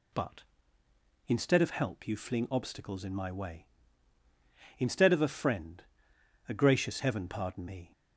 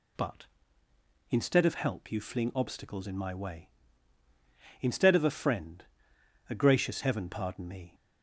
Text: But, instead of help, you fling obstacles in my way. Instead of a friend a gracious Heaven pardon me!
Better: neither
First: pauses between "friend" and "a"; noticeable; at 5.8 s; 0.64 s long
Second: pauses between "friend" and "a"; noticeable; at 5.8 s; 0.64 s long

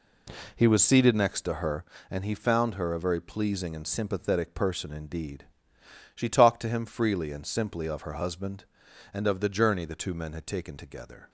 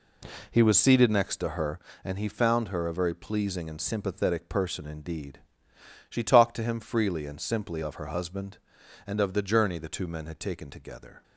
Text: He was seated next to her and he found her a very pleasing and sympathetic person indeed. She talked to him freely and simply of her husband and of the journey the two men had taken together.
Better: neither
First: none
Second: none

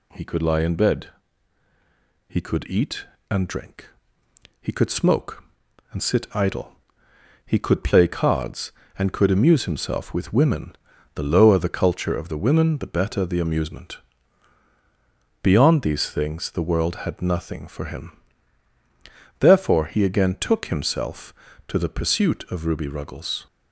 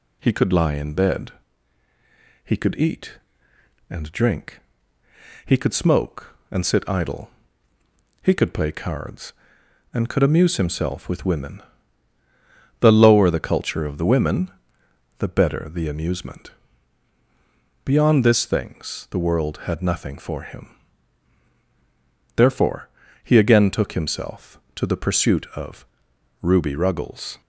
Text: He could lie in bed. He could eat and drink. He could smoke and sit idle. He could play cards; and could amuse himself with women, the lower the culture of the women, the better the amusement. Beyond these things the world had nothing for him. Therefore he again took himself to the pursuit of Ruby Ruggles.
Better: first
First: none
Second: says "this" for "these"; at 18.2 s // pauses between "Therefore" and "he"; slight; at 22.8 s; 0.36 s long // pauses between "of" and "Ruby"; noticeable; at 25.8 s; 0.56 s long

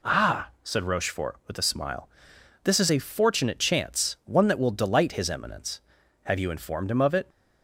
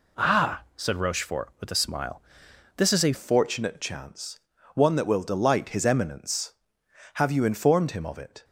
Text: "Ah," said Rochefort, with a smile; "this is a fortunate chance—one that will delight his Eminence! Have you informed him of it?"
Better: first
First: none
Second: changes voice at "fortunate"; from 3.1 s on; 5.3 s long

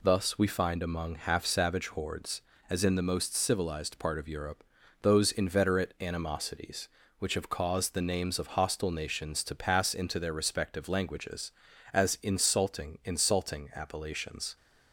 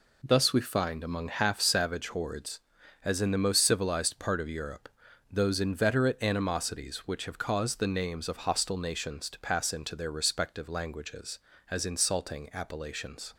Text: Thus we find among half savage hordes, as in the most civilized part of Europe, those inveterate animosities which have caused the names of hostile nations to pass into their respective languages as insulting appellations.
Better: second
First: says "insulting" twice; at 13.0 s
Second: none

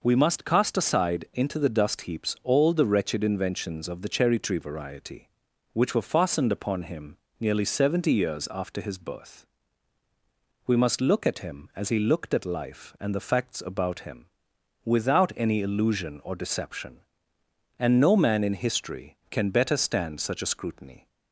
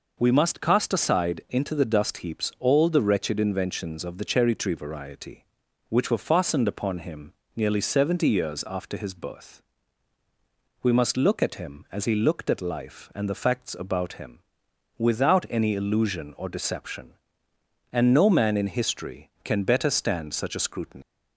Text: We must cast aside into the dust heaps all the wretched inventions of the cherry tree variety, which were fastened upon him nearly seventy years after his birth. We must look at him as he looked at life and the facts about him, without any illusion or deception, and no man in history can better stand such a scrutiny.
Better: first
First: pauses between "him" and "nearly"; slight; at 7.1 s; 0.22 s long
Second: pauses between "him" and "nearly"; slight; at 7.3 s; 0.22 s long // leaves "scrutiny" unfinished; at 21.0 s; 180 ms

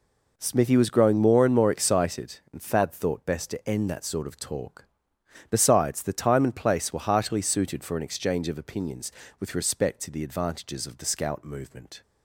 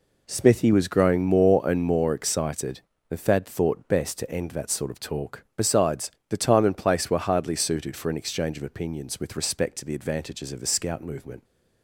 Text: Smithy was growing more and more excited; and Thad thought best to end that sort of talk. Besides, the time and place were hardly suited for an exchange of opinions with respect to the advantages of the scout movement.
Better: second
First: says "heartily" for "hardly"; at 6.9 s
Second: none

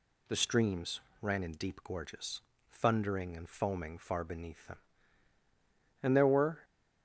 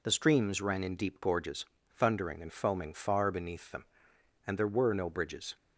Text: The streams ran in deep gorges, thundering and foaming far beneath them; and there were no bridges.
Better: second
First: pauses between "streams" and "ran"; slight; at 1.0 s; 0.18 s long // stops before "no bridges"; at 6.6 s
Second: none

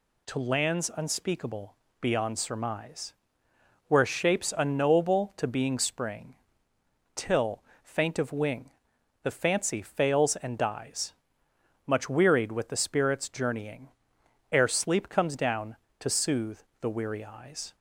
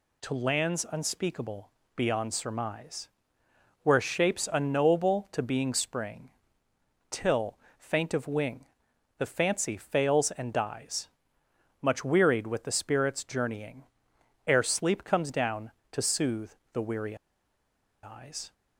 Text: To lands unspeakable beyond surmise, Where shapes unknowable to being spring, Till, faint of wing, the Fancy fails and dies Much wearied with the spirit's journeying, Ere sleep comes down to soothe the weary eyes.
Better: first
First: pauses between "unspeakable" and "beyond"; slight; at 1.7 s; 0.24 s long // pauses between "dies" and "Much"; noticeable; at 11.1 s; 0.72 s long // pauses between "soothe" and "the"; slight; at 16.6 s; 0.20 s long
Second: pauses between "unspeakable" and "beyond"; slight; at 1.7 s; 0.24 s long // pauses between "dies" and "Much"; noticeable; at 11.0 s; 0.72 s long // pauses between "soothe" and "the"; slight; at 16.5 s; 0.20 s long // pauses between "weary" and "eyes"; noticeable; at 17.1 s; 0.88 s long

